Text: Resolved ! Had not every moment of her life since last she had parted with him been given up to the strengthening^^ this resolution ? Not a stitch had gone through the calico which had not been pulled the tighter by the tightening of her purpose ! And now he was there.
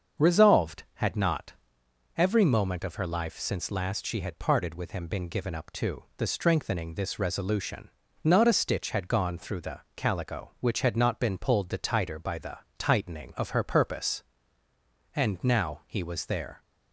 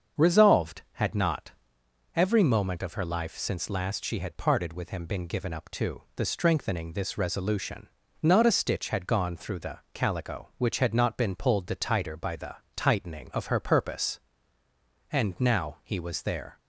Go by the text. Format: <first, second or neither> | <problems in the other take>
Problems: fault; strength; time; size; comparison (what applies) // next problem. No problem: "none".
neither | starts louder than the rest; the same in both // pauses between "not" and "every"; noticeable; the same in both // pauses between "the" and "tightening"; slight; the same in both